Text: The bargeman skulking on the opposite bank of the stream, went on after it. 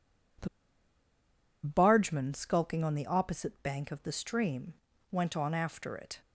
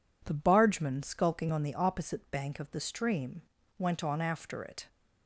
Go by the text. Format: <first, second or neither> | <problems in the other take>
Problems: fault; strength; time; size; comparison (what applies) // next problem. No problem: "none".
second | pauses between "The" and "bargeman"; at 0.4 s; 1.1 s long